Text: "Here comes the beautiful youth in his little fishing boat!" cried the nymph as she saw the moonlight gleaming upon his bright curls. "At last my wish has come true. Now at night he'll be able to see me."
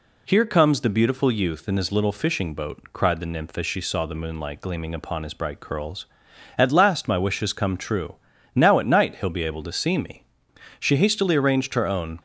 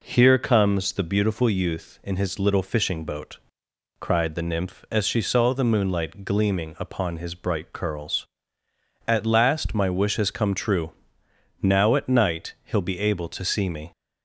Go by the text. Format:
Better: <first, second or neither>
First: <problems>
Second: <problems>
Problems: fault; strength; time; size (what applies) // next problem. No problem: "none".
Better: second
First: goes on to say "She hastily arranged her own"; from 10.7 s on; 1.3 s long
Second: none